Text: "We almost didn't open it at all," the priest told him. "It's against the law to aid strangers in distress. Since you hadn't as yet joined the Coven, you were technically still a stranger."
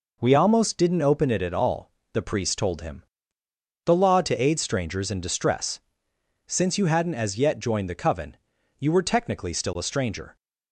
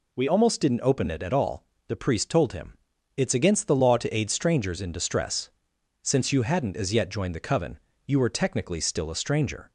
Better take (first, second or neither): second